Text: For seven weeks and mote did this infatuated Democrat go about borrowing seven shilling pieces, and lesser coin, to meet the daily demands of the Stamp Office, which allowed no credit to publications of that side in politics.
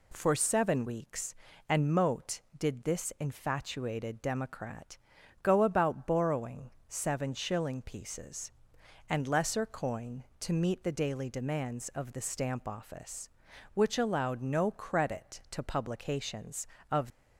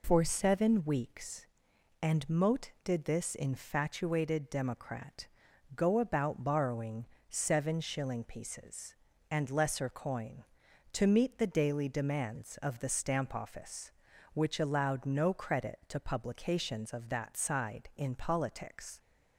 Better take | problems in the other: second | pauses between "Democrat" and "go"; at 4.9 s; 0.44 s long; noticeable in the second // pauses between "borrowing" and "seven"; slight; at 6.6 s; 0.20 s long; slight in the second // stops before "that side in politics"; at 17.1 s

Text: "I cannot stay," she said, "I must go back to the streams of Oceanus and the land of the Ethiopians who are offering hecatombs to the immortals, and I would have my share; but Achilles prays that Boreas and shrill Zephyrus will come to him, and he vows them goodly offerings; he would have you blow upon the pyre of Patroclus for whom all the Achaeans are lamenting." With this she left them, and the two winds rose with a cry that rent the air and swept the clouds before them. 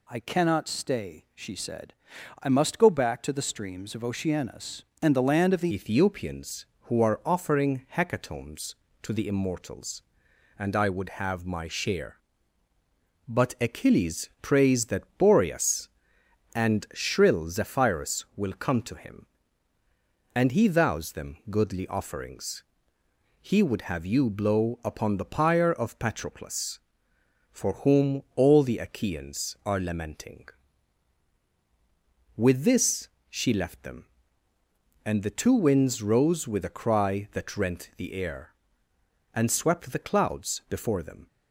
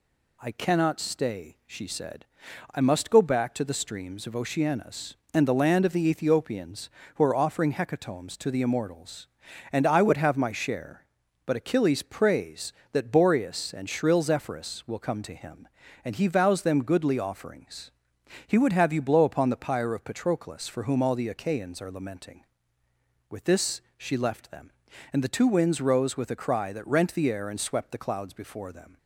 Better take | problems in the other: second | changes voice at "Ethiopians"; from 5.7 s on; 35.5 s long // pauses between "this" and "she"; slight; at 33.0 s; 0.22 s long; slight in the second

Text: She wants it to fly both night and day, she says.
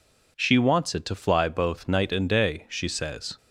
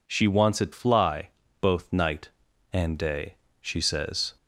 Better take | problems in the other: first | skips "to"; at 0.7 s // pauses between "fly" and "both"; slight; at 1.2 s; 0.32 s long

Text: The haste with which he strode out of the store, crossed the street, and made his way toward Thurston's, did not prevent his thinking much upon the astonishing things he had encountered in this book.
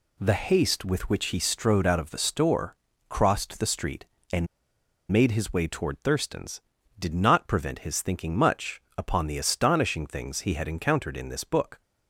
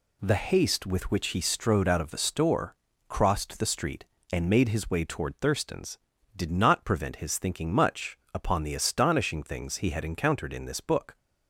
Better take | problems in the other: second | pauses between "and" and "made"; noticeable; at 4.4 s; 0.64 s long // pauses between "much" and "upon"; slight; at 8.8 s; 0.16 s long; slight in the second

